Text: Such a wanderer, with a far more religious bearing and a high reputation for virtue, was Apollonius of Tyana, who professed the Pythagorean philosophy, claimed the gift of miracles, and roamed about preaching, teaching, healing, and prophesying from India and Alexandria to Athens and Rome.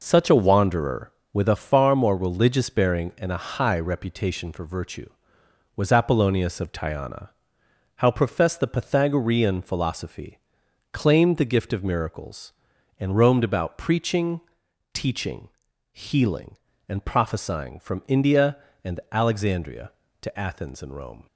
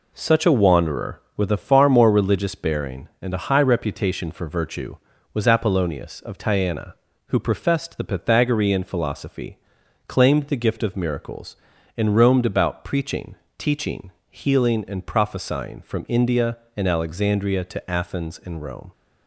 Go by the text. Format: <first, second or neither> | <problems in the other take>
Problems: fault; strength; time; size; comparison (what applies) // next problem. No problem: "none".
second | says "how" for "who"; at 7.9 s